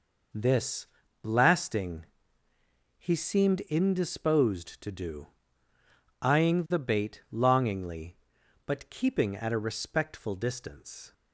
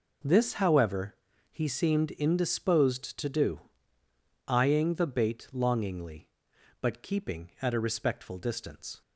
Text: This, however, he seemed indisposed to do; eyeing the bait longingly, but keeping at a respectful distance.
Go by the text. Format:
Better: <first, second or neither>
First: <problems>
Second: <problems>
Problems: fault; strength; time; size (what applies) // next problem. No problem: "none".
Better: second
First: says "blasting" for "however"; at 1.2 s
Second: none